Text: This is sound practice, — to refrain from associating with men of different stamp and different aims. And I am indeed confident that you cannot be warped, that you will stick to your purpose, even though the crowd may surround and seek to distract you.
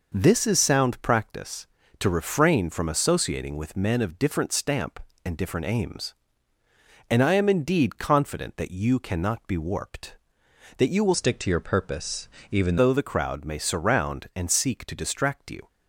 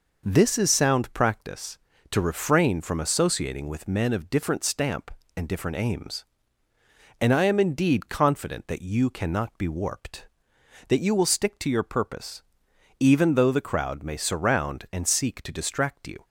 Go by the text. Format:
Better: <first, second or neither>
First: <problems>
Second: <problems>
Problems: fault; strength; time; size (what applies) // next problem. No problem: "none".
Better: second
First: changes voice from "stick" to "even"; from 11.1 to 12.7 s; 1.6 s long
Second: none